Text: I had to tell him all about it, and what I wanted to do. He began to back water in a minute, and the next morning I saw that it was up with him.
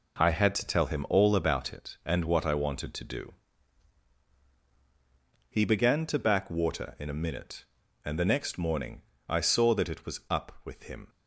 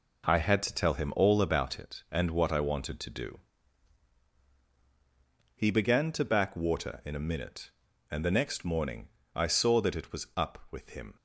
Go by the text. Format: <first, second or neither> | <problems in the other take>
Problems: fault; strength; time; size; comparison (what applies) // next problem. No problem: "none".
neither | pauses between "morning" and "I"; slight; the same in both